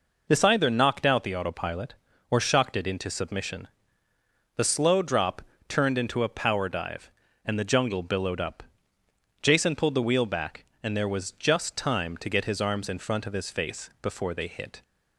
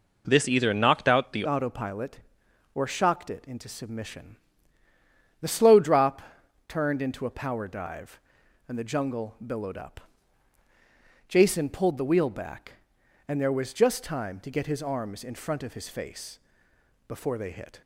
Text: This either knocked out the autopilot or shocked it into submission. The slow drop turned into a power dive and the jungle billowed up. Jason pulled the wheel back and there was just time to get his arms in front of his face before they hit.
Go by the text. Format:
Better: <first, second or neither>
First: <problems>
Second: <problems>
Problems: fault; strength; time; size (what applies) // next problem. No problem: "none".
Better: first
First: pauses between "drop" and "turned"; slight; at 5.4 s; 0.26 s long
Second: changes voice at "autopilot"; from 1.4 s on; 16.4 s long // pauses between "drop" and "turned"; noticeable; at 6.2 s; 0.46 s long // pauses between "face" and "before"; noticeable; at 16.3 s; 0.68 s long